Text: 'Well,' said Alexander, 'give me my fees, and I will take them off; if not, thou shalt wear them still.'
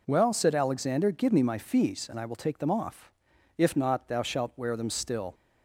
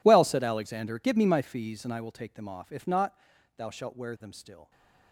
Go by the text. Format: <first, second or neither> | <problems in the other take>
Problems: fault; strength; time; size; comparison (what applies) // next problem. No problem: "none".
first | gets quieter; strong; throughout; 20.5 dB